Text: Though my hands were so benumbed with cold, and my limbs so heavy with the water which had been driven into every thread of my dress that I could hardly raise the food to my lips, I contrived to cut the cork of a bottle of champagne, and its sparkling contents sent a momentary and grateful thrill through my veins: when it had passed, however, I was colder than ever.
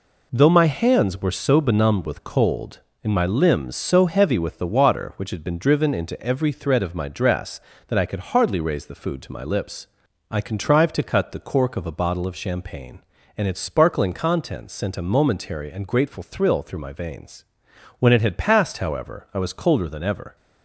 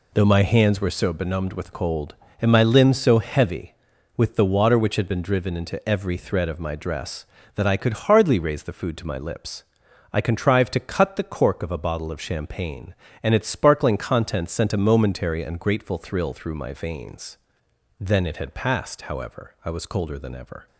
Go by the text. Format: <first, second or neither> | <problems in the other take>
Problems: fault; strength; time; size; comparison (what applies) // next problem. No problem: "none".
first | says "then" for "when"; at 18.0 s